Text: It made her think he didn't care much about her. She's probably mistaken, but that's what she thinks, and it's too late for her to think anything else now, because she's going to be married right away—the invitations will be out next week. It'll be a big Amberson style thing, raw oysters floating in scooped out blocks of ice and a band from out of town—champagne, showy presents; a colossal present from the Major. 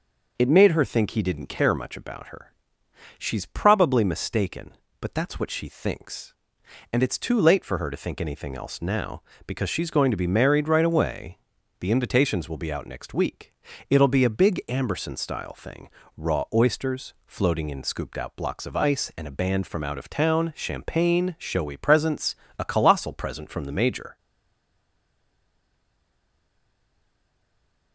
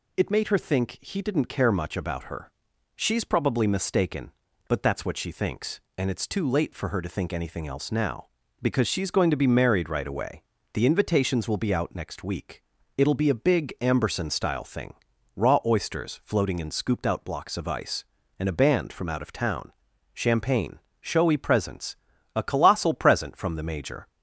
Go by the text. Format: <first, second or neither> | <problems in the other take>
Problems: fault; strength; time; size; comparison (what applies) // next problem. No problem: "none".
second | stays silent after the last word; strong; from 24.1 s on; 3.8 s long